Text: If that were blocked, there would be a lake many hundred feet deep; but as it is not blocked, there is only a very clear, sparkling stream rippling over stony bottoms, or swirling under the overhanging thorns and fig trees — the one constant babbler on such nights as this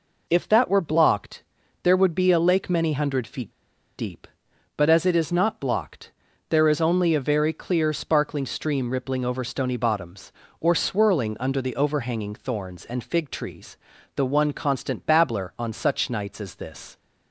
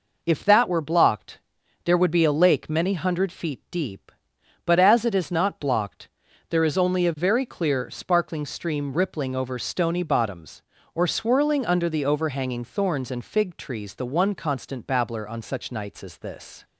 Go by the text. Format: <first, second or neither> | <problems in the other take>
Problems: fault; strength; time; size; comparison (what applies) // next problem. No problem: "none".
second | pauses between "feet" and "deep"; noticeable; at 3.4 s; 0.47 s long